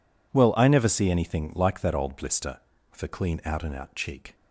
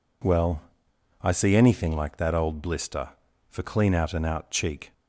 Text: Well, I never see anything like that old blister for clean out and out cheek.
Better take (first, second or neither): first